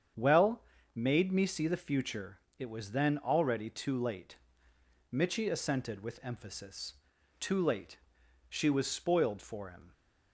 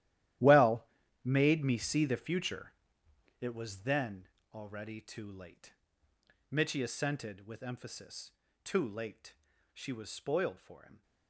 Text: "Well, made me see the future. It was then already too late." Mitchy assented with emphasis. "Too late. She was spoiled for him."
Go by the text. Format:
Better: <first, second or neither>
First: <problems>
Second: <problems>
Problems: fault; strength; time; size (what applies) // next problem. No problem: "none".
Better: first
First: starts louder than the rest; strong; until 1.4 s; 8 dB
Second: gets quieter; strong; throughout; 13.5 dB // starts louder than the rest; strong; until 1.7 s; 13.5 dB // pauses between "then" and "already"; slight; at 4.2 s; 0.26 s long